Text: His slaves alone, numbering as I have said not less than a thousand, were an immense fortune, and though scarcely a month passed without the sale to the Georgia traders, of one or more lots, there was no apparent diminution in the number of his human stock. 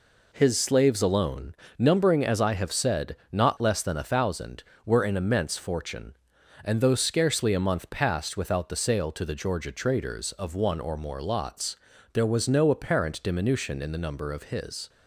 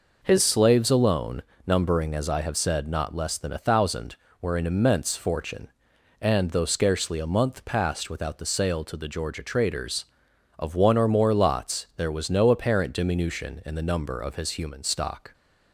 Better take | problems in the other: second | pauses between "said" and "not"; slight; at 3.1 s; 0.16 s long // stops before "human stock"; at 14.8 s

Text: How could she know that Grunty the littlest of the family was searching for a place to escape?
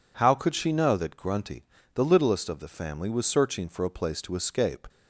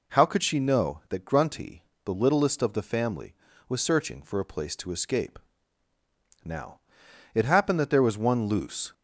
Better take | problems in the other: first | pauses between "Grunty" and "the"; slight; at 1.8 s; 0.22 s long; slight in the first // goes on to say "Now it happened that there was one loose"; strong; from 6.4 s on; 2.5 s long

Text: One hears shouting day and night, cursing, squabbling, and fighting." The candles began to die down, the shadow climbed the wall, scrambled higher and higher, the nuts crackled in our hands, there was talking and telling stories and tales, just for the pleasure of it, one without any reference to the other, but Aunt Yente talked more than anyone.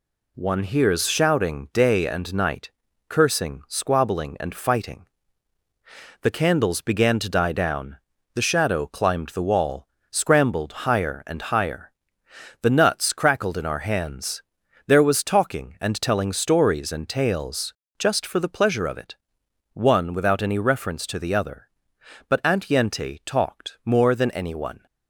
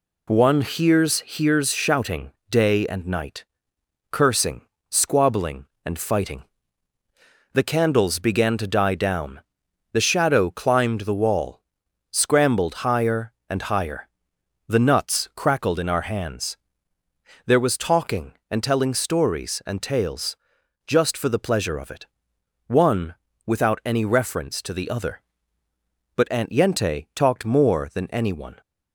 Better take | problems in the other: first | says "hears" twice; at 1.2 s // pauses between "shouting" and "day"; slight; at 2.3 s; 0.18 s long // pauses between "one" and "without"; slight; at 23.1 s; 0.32 s long

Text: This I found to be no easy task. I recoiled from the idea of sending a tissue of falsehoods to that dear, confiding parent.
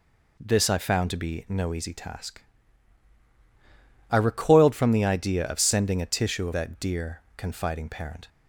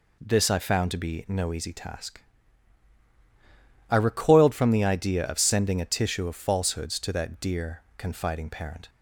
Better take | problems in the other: second | skips "falsehoods to"; at 6.5 s

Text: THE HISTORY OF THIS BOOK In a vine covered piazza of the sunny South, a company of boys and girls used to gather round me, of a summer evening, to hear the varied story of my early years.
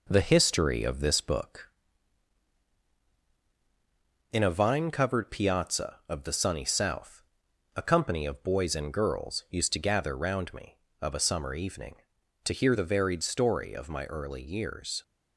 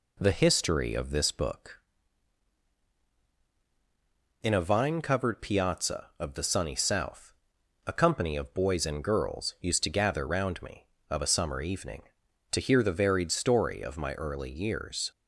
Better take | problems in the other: second | gets quieter; slight; throughout; 3 dB

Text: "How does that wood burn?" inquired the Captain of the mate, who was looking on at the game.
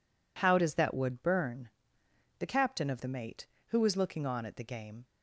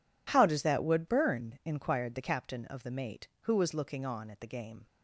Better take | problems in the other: second | skips "inquired"; at 2.0 s

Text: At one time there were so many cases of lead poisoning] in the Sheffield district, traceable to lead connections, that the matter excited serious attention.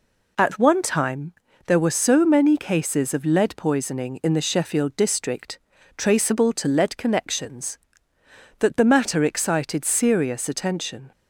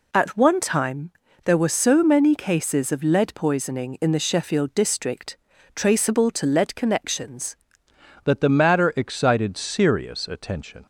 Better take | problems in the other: first | pauses between "time" and "there"; slight; at 1.1 s; 0.34 s long; slight in the first // changes voice at "that"; from 8.2 s on; 2.6 s long

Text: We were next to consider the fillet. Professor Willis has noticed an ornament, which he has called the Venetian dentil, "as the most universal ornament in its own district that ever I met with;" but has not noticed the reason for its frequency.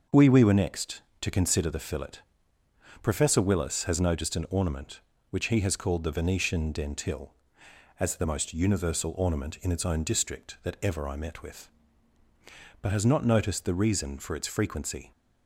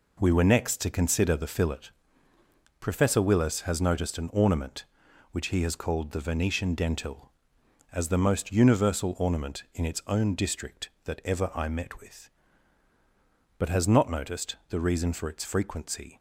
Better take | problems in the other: second | starts louder than the rest; noticeable; until 1.2 s; 6 dB // says "We" twice; at 0.2 s

